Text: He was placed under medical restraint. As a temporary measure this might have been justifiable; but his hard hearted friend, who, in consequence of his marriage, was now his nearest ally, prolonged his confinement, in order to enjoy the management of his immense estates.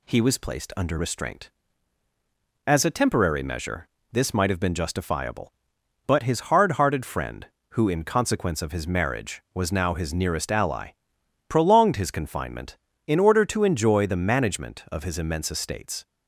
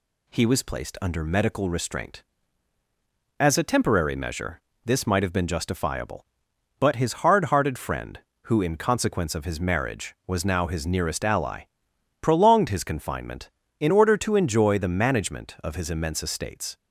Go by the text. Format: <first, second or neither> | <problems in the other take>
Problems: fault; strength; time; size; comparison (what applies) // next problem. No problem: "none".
second | skips "medical"; at 0.9 s // pauses between "measure" and "this"; slight; at 3.8 s; 0.22 s long; slight in the second